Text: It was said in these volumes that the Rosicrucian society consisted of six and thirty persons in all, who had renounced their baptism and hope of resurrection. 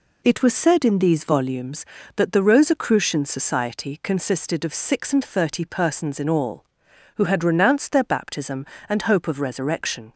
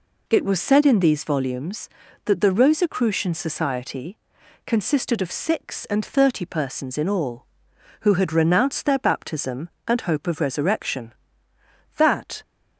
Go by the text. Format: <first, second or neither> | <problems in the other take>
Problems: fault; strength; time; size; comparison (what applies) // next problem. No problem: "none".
first | pauses between "society" and "consisted"; noticeable; at 4.1 s; 0.48 s long // goes on to say "That"; slight; from 11.9 s on; 0.44 s long